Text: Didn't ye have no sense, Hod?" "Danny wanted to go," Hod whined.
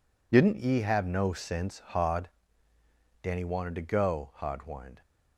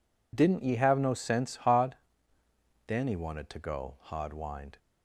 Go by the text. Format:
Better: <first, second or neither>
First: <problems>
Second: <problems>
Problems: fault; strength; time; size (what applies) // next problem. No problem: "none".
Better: neither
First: none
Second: none